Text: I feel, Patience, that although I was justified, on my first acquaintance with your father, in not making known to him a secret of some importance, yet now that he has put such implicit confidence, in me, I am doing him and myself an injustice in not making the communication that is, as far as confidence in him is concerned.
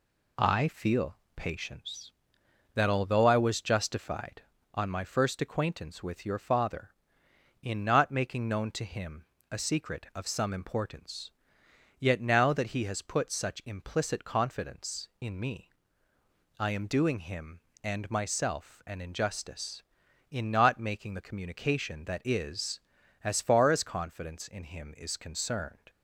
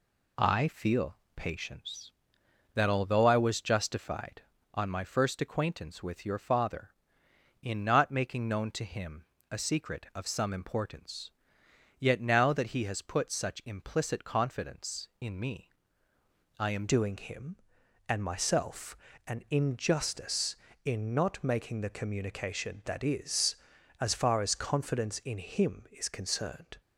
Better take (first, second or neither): first